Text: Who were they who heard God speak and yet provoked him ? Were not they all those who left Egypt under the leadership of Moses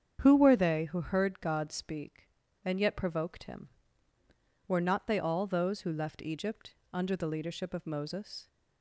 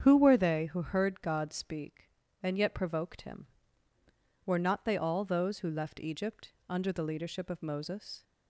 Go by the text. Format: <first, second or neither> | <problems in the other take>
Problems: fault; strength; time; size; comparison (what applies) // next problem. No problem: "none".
neither | starts louder than the rest; strong; the same in both // pauses between "Egypt" and "under"; slight; the same in both